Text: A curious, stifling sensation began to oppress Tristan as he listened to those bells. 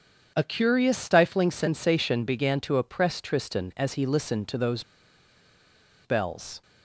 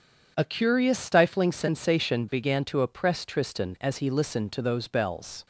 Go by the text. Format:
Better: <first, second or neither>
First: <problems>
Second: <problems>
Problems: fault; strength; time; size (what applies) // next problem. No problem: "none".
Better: second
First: pauses between "those" and "bells"; at 4.8 s; 1.2 s long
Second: none